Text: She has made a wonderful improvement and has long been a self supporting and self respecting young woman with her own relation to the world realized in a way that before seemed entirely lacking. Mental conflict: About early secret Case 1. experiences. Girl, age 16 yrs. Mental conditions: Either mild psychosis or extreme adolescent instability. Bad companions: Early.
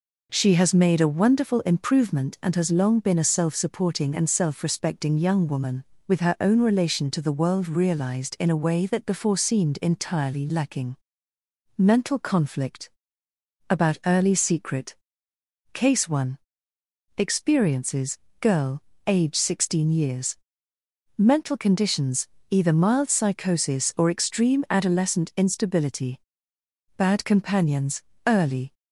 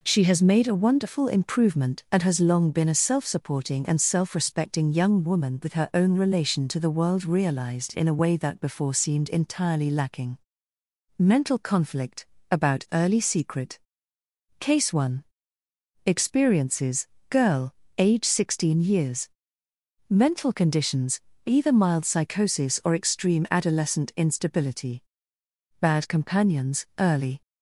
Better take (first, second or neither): neither